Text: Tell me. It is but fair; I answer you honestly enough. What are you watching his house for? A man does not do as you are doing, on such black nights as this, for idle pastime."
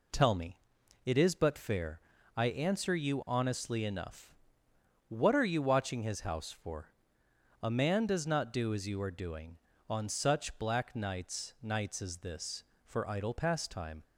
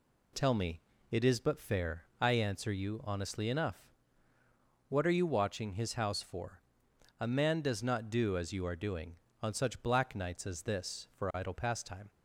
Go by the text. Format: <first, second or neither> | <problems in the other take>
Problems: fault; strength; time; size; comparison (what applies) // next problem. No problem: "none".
second | says "nights" twice; at 11.6 s